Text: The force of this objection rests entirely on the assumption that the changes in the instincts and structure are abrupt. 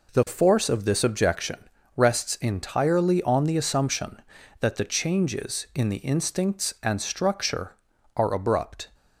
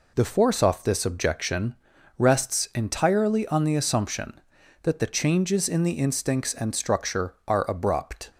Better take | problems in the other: first | says "off" for "of"; at 0.6 s // pauses between "objection" and "rests"; at 1.7 s; 0.42 s long; also in the first

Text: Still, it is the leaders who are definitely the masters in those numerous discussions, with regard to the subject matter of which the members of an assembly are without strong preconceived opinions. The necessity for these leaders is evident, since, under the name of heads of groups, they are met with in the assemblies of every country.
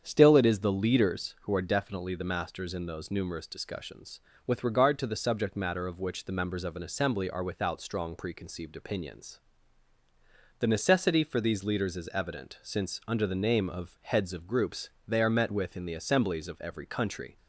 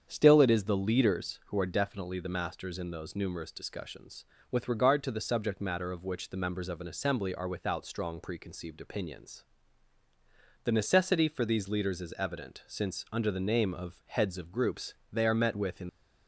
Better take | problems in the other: first | starts louder than the rest; strong; until 1.0 s; 7.5 dB; strong in the first // stops before "the assemblies of every country"; at 15.8 s

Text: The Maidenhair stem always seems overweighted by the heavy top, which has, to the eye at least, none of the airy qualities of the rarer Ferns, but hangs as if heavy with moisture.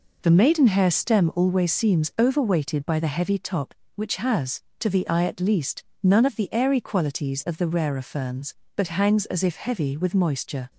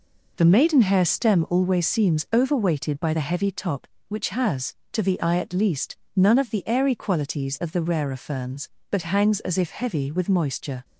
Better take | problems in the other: neither | none

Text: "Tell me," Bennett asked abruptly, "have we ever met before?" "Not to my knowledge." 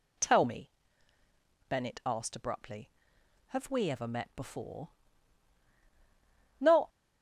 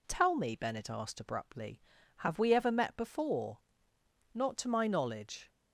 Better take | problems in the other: second | stops before "to my knowledge"; at 6.8 s

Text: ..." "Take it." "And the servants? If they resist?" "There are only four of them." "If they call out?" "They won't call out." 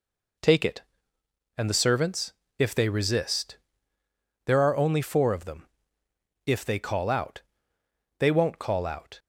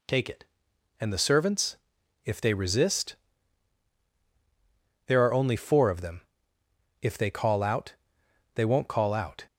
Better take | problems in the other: neither | none

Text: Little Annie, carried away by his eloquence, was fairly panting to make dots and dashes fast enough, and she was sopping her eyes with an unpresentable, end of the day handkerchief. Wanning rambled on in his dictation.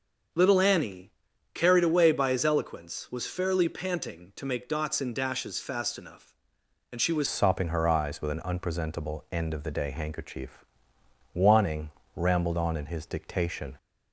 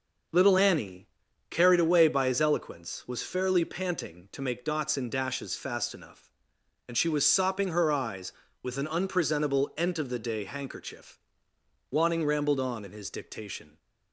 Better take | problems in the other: second | starts louder than the rest; until 1.7 s; 6.5 dB // changes voice at "sopping"; from 7.2 s on; 6.5 s long // pauses between "Wanning" and "rambled"; slight; at 11.9 s; 0.26 s long

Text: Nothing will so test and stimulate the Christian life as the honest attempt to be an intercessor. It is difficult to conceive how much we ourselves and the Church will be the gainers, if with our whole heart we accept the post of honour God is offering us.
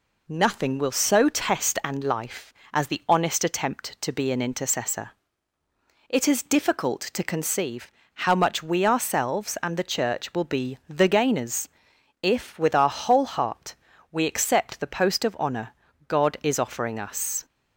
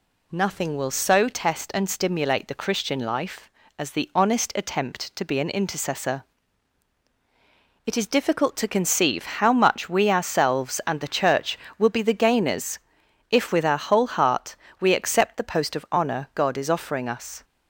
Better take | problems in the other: second | skips "stimulate the Christian"; at 2.0 s // pauses between "conceive" and "how"; slight; at 7.9 s; 0.22 s long // pauses between "heart" and "we"; slight; at 13.7 s; 0.36 s long; slight in the second // pauses between "honour" and "God"; at 15.7 s; 0.38 s long

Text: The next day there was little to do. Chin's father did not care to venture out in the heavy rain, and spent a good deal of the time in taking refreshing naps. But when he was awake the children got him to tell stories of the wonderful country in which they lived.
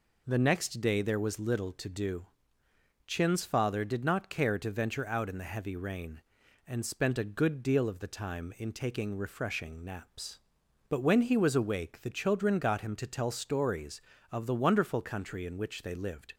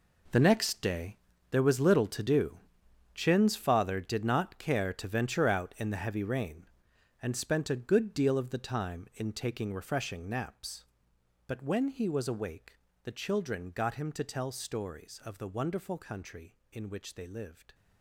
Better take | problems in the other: first | gets quieter; strong; throughout; 13.5 dB // pauses between "day" and "there"; slight; at 1.1 s; 0.34 s long // pauses between "awake" and "the"; slight; at 12.7 s; 0.32 s long

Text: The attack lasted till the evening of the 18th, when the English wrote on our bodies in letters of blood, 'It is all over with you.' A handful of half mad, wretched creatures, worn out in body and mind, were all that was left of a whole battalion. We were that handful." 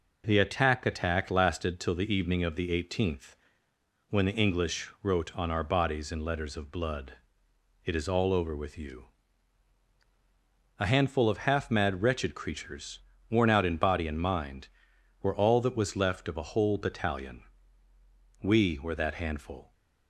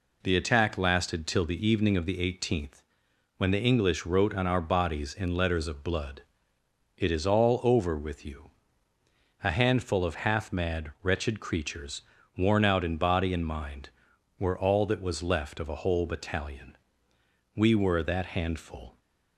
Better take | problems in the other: second | says "attack" twice; at 0.8 s

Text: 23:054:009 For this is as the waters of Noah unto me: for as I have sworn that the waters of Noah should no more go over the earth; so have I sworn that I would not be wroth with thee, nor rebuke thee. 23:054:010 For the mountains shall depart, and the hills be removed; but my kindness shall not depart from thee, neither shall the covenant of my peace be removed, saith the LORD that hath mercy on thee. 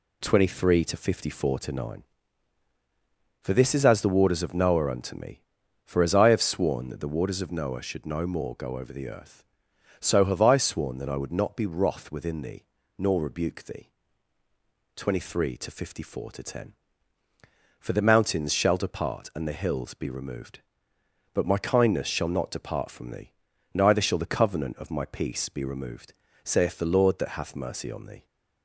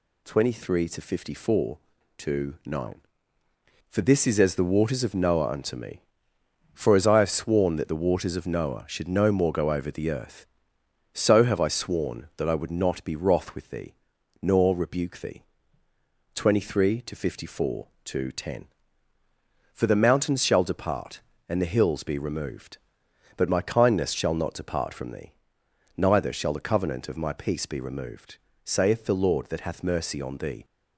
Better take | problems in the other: second | says "within" for "with"; at 12.1 s

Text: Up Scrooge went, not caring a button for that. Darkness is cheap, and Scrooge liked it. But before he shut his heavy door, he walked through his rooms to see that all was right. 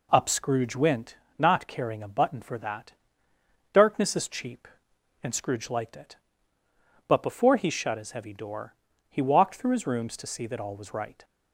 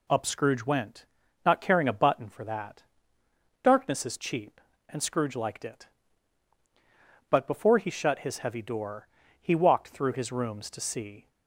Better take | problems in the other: first | stops before "that all was right"; at 11.2 s

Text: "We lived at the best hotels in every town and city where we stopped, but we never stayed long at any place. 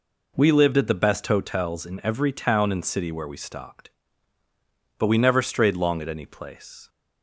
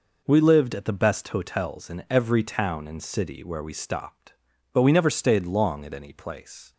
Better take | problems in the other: second | says "strayed" for "stayed"; at 5.4 s

